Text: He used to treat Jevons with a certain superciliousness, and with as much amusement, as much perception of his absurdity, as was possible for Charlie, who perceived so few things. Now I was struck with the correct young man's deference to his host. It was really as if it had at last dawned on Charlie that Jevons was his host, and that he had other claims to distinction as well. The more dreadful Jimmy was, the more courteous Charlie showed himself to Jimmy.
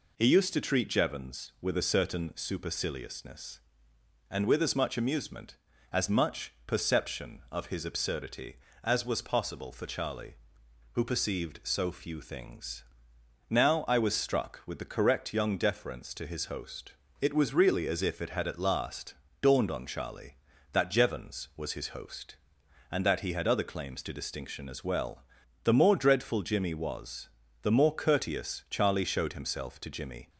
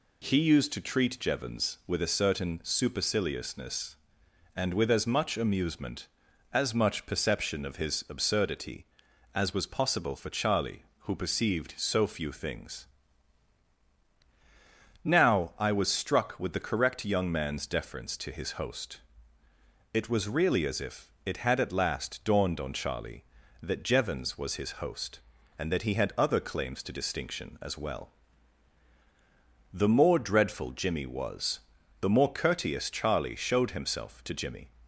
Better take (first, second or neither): second